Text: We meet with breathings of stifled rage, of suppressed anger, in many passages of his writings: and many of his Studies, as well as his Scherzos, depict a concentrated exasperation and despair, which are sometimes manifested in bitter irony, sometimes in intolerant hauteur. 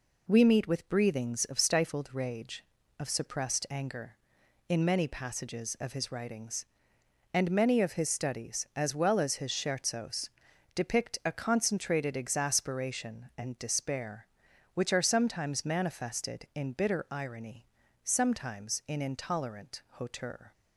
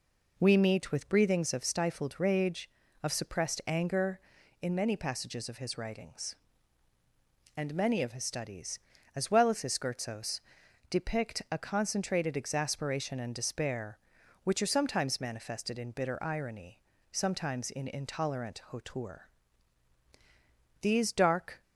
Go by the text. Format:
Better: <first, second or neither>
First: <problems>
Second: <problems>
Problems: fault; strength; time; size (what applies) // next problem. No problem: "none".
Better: first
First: none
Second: goes on to say "These dark"; noticeable; from 20.8 s on; 0.80 s long